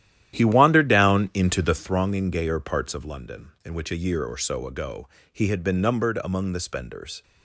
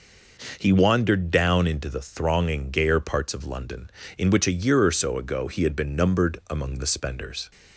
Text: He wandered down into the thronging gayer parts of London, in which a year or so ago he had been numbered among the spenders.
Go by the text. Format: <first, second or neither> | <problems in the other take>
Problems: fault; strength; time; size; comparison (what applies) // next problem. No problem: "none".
second | starts louder than the rest; strong; until 2.0 s; 12 dB // pauses between "ago" and "he"; slight; at 5.0 s; 0.26 s long